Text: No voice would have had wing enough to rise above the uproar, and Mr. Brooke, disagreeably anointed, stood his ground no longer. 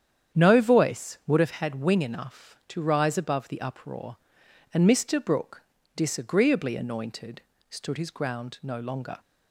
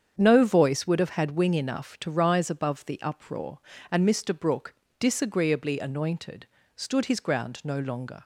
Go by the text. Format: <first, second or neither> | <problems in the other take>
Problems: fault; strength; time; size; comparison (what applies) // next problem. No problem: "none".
neither | starts louder than the rest; strong; the same in both